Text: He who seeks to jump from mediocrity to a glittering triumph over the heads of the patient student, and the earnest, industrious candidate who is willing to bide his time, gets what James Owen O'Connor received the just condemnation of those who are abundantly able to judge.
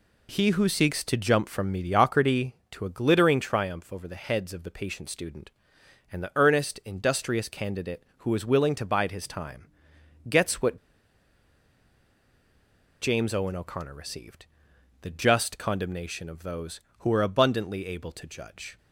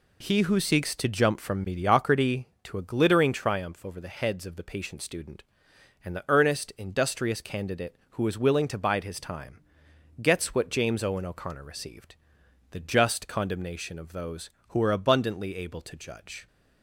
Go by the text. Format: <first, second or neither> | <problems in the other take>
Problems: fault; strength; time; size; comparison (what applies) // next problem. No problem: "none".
second | pauses between "what" and "James"; strong; at 10.7 s; 2.2 s long // pauses between "received" and "the"; noticeable; at 14.4 s; 0.56 s long; noticeable in the second